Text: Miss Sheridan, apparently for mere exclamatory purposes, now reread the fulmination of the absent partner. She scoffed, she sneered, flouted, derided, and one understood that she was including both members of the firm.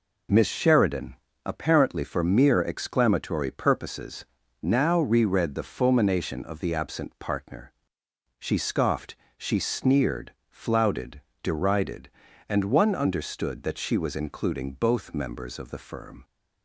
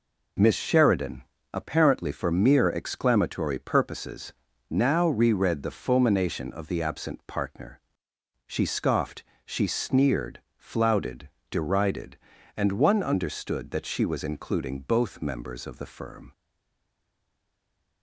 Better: first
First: none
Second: stays silent after the last word; noticeable; from 16.3 s on; 1.7 s long

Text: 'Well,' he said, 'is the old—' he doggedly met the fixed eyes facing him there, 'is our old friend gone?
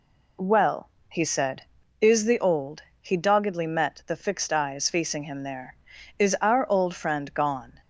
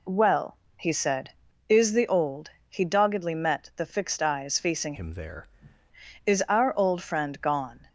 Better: first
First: none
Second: changes voice from "him" to "there"; from 4.9 to 5.4 s; 0.5 s long

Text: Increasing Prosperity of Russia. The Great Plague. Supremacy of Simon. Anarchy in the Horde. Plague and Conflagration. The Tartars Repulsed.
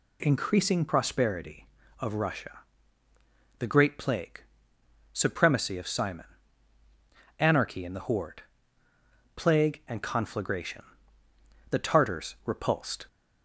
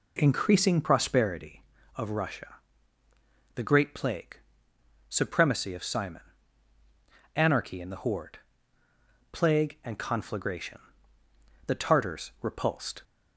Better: first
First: none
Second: starts louder than the rest; slight; until 1.5 s; 3.5 dB

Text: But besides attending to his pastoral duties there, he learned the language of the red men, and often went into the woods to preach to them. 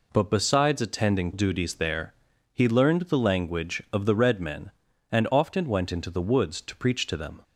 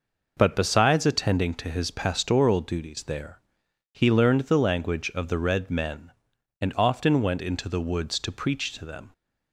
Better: second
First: skips "to his pastoral"; at 1.3 s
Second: none

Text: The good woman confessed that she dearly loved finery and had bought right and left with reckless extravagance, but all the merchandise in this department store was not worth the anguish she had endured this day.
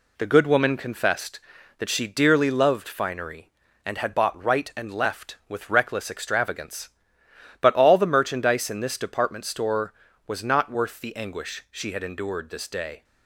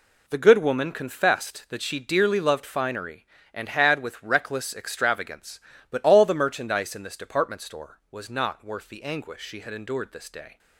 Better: first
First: none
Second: skips "bought right and left"; at 4.0 s

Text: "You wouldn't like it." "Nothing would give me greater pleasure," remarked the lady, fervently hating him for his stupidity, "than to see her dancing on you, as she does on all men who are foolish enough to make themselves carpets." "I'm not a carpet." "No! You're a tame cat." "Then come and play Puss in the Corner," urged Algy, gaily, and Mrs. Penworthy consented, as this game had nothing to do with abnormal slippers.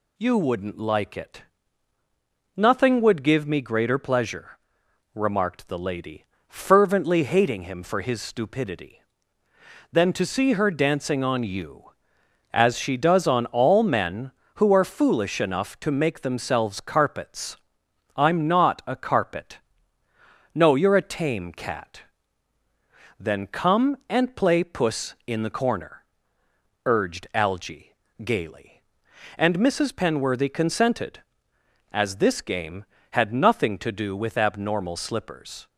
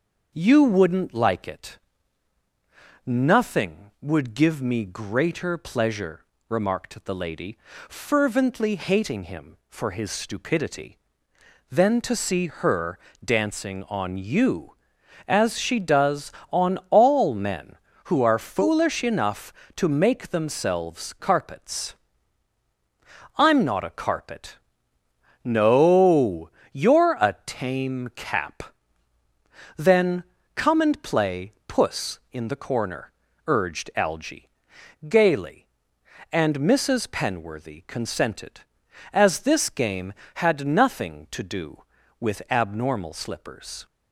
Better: first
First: none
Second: starts louder than the rest; until 1.3 s; 6.5 dB // pauses between "her" and "dancing"; slight; at 12.9 s; 0.24 s long // says "cap" for "cat"; at 28.1 s // pauses between "Then" and "come"; slight; at 30.2 s; 0.32 s long

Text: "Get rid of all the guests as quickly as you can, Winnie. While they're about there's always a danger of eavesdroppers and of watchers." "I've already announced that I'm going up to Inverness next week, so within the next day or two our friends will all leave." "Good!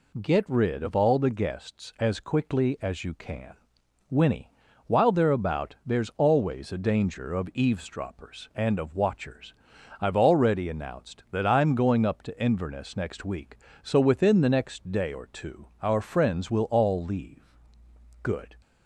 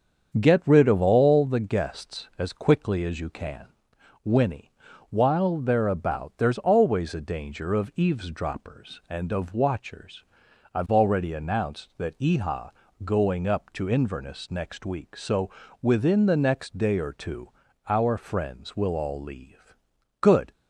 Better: first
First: none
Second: starts louder than the rest; strong; until 1.4 s; 7 dB // says "Eha" for "I'm"; at 12.1 s // pauses between "so" and "within"; slight; at 15.5 s; 0.30 s long // pauses between "two" and "our"; slight; at 17.5 s; 0.36 s long

